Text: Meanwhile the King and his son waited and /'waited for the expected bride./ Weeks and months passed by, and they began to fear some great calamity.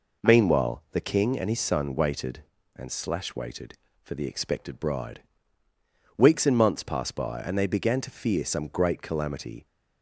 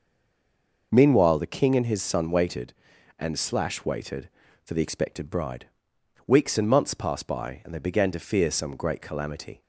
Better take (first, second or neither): first